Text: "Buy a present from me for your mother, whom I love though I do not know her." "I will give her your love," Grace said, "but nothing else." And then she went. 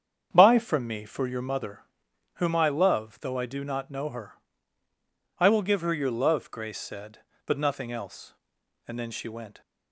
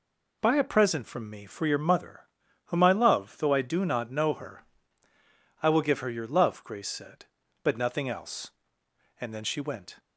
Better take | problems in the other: second | starts louder than the rest; strong; until 1.3 s; 8 dB // skips "a present"; at 0.5 s

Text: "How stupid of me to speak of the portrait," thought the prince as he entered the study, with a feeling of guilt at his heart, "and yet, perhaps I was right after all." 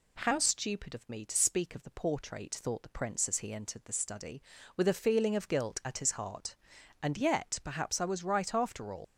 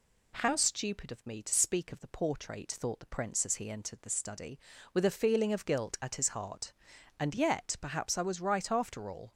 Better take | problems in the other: second | leaves "all" unfinished; at 9.0 s; 105 ms

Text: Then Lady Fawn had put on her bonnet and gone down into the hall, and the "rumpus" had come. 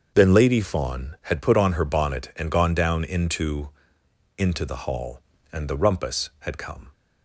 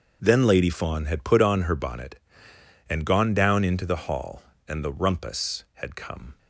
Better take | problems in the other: second | starts louder than the rest; until 1.1 s; 6.5 dB; also in the second // says "into" twice; at 4.3 s

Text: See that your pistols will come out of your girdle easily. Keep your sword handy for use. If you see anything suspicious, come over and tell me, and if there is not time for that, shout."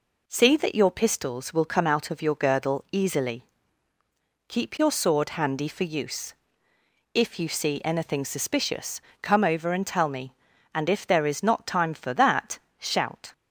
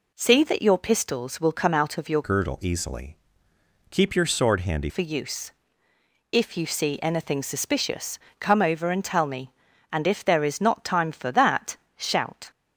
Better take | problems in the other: first | changes voice from "girdle" to "handy"; from 2.2 to 4.8 s; 2.6 s long

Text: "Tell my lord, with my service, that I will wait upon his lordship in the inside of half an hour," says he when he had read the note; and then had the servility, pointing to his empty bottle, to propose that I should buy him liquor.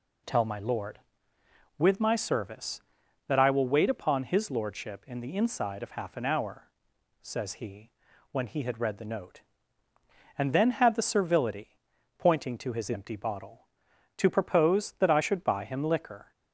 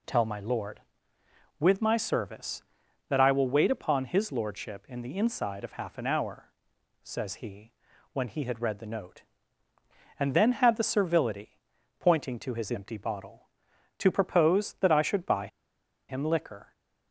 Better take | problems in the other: first | pauses between "he" and "when"; at 7.7 s; 0.42 s long; also in the first // pauses between "buy" and "him"; noticeable; at 15.4 s; 0.61 s long

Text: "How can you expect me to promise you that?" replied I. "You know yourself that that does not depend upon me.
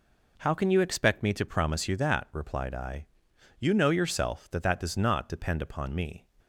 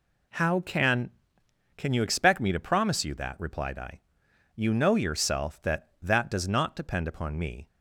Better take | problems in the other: first | says "can" twice; at 1.7 s

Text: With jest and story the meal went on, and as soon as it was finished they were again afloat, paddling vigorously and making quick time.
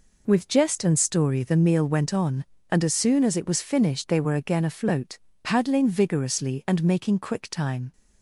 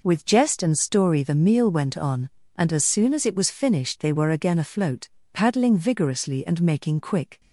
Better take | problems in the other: first | stops before "time"; at 7.4 s

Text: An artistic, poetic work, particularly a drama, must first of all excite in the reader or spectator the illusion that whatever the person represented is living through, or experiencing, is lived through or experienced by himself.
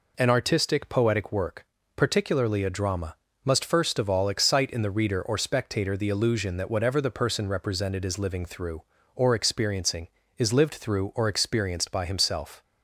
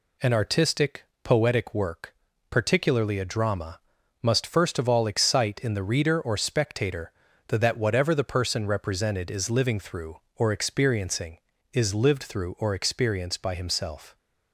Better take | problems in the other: first | pauses between "spectator" and "the"; at 7.1 s; 0.38 s long // skips "illusion"; at 7.5 s

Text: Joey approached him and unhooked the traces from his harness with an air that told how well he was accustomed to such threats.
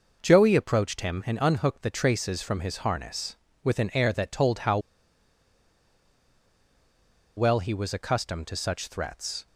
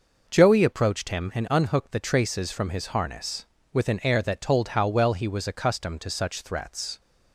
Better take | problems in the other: second | pauses between "how" and "well"; strong; at 4.7 s; 2.5 s long

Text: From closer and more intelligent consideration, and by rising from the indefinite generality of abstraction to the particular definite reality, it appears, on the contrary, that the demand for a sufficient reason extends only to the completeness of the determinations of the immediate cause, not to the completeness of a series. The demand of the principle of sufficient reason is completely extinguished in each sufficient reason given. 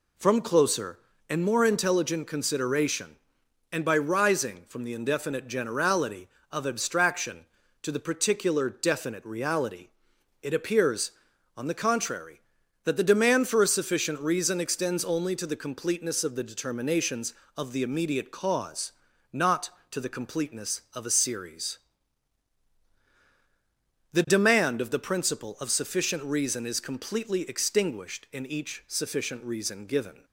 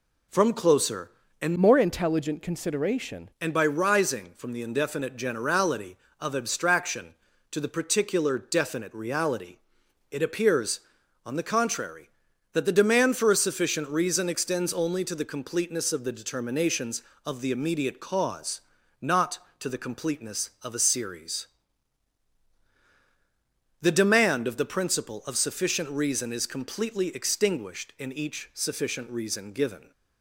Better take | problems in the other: first | changes voice from "more" to "consideration"; from 1.5 to 3.2 s; 1.7 s long

